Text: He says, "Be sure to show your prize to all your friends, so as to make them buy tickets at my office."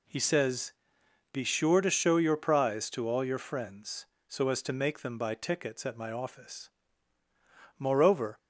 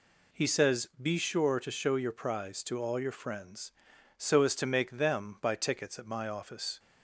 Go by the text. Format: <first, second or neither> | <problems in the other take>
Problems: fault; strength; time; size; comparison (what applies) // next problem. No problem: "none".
second | goes on to say "Moreover"; from 7.7 s on; 0.58 s long